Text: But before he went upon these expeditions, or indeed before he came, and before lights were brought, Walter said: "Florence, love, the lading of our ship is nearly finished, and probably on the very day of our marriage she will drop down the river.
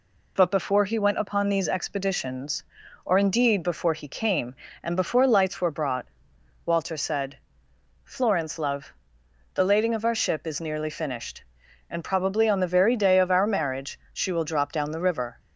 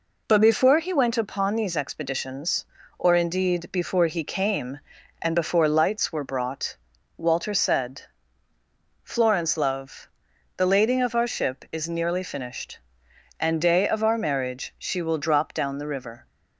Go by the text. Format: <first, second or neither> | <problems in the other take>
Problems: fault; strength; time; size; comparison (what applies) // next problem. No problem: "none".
first | skips "probably on the very"; at 13.5 s